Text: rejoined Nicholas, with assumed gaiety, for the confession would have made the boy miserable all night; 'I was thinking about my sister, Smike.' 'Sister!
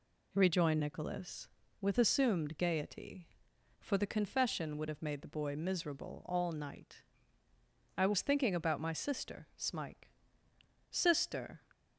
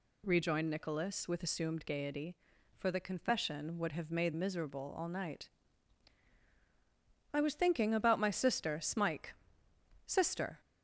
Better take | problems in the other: first | skips "the boy"; at 4.3 s

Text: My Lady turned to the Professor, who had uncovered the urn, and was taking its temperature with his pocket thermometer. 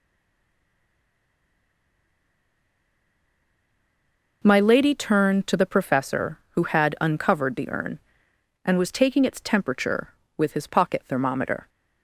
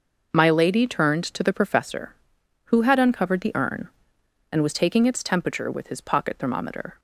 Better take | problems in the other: second | stays silent before the first word; strong; until 4.4 s; 4.4 s long

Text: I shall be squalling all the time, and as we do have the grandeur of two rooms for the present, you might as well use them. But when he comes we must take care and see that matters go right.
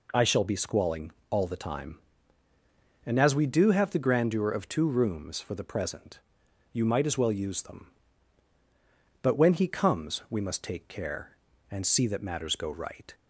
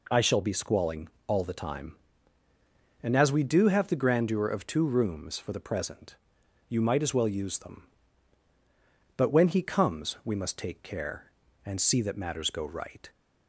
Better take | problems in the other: neither | pauses between "squalling" and "all"; slight; the same in both

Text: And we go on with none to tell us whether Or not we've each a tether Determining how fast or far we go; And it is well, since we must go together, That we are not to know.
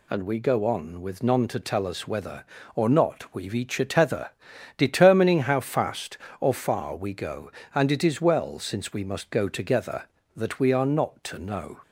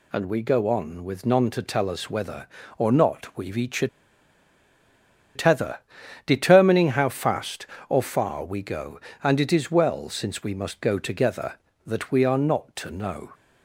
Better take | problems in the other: first | pauses between "a" and "tether"; strong; at 3.8 s; 1.4 s long // pauses between "tether" and "Determining"; noticeable; at 5.7 s; 0.46 s long; noticeable in the first

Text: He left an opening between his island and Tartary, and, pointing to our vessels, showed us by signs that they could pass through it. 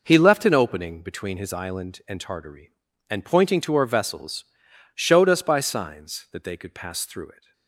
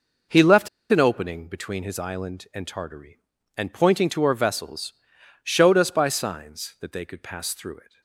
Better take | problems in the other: first | pauses between "left" and "an"; slight; at 0.6 s; 0.21 s long

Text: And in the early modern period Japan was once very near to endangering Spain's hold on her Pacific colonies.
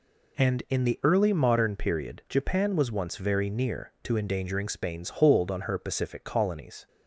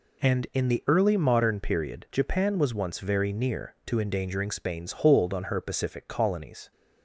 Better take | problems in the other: neither | none

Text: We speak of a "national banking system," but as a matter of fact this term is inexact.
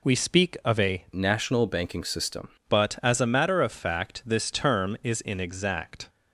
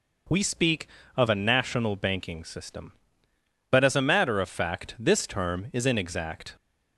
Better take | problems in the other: second | changes voice from "national" to "system"; from 1.1 to 2.4 s; 1.3 s long

